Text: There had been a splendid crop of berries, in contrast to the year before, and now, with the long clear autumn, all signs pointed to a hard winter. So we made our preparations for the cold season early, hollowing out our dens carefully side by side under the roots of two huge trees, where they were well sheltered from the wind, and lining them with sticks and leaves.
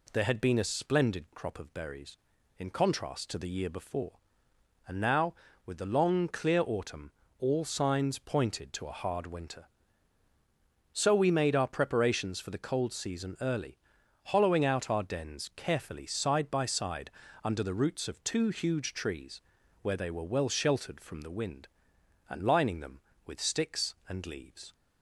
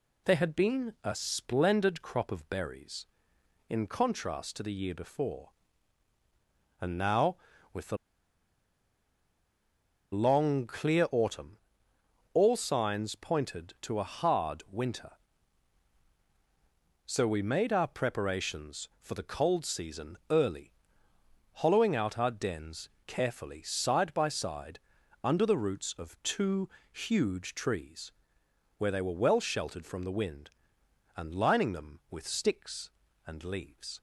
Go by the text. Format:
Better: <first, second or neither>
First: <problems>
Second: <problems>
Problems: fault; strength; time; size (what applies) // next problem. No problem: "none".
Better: first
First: pauses between "side" and "under"; slight; at 17.0 s; 0.36 s long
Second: pauses between "the" and "long"; strong; at 7.9 s; 2.1 s long // pauses between "dens" and "carefully"; slight; at 22.8 s; 0.20 s long // pauses between "side" and "under"; at 24.7 s; 0.44 s long // pauses between "two" and "huge"; slight; at 26.6 s; 0.24 s long